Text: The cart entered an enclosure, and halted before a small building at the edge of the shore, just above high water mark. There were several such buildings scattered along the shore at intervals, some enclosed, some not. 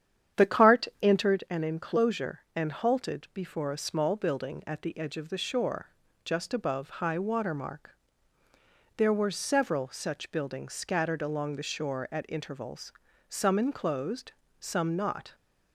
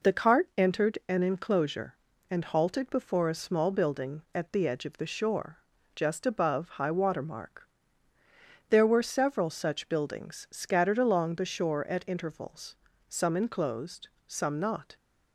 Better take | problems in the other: second | starts louder than the rest; strong; until 1.4 s; 9.5 dB

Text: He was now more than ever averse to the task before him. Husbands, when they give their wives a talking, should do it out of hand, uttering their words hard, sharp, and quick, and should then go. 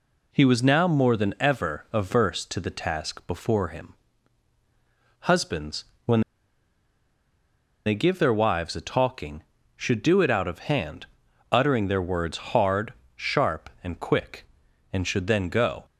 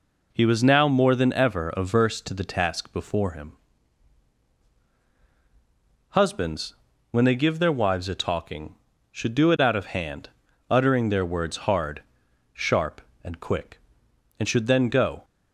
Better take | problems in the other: second | pauses between "when" and "they"; strong; at 6.2 s; 1.6 s long

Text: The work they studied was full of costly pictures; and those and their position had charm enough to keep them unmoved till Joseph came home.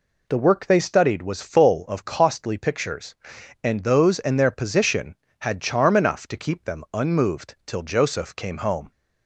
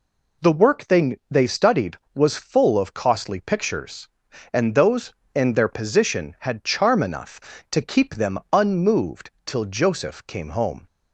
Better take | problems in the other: first | says "they" twice; at 1.2 s // pauses between "unmoved" and "till"; slight; at 9.3 s; 0.16 s long

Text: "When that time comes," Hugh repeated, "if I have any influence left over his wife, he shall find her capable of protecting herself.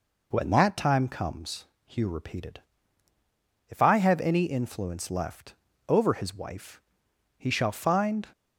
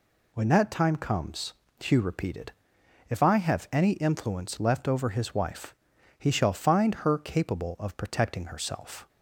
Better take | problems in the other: second | pauses between "left" and "over"; slight; at 5.5 s; 0.34 s long // stops before "her capable of protecting herself"; at 8.3 s

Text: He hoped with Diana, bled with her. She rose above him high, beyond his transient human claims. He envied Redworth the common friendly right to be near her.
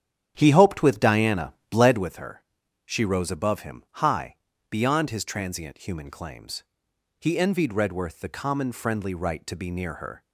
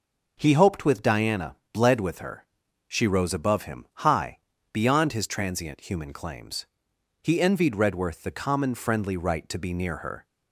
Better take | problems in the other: second | starts louder than the rest; strong; until 2.1 s; 10 dB // pauses between "him" and "high"; slight; at 3.8 s; 0.18 s long; slight in the second

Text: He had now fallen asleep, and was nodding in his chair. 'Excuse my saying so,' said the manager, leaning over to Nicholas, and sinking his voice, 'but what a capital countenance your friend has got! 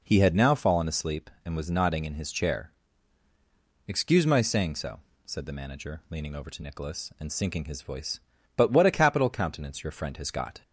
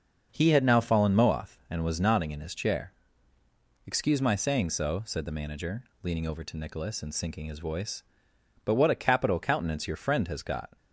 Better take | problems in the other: first | starts louder than the rest; until 1.3 s; 6 dB // says "moath" for "asleep"; at 1.1 s

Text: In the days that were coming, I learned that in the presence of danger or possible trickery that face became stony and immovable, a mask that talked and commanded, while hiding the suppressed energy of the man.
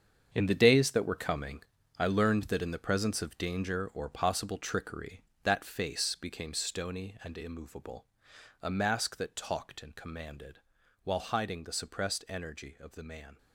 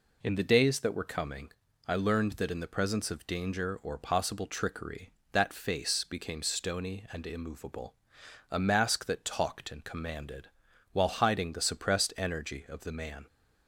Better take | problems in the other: second | gets quieter; strong; throughout; 11.5 dB

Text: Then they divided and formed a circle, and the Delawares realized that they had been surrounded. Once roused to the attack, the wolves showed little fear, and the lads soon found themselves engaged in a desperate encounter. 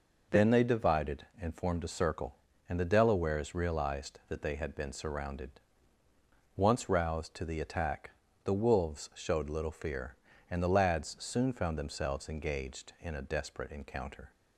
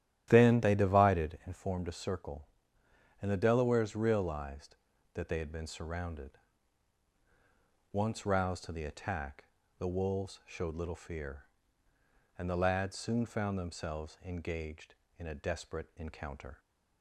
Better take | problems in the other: first | starts louder than the rest; strong; until 1.4 s; 11.5 dB

